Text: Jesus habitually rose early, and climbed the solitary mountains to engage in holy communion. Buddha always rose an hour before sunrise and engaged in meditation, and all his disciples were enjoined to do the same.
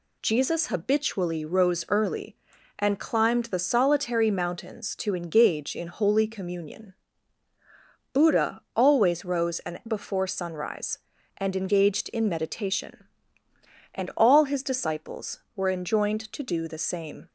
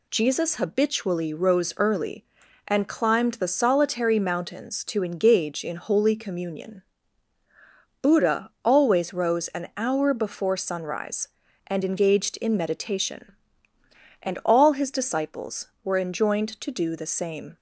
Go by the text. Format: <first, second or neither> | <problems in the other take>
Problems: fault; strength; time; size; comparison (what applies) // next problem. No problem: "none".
second | skips "hour"; at 9.8 s